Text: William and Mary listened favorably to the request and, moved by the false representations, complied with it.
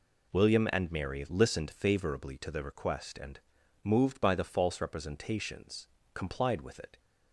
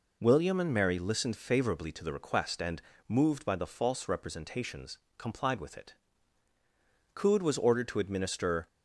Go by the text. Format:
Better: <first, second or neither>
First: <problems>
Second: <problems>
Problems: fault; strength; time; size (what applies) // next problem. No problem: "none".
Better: first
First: none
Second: goes on to say "Coode was ordered to administer"; from 7.1 s on; 1.5 s long